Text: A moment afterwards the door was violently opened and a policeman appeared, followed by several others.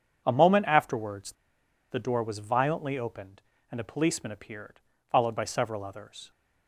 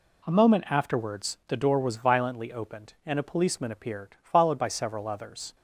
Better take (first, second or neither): second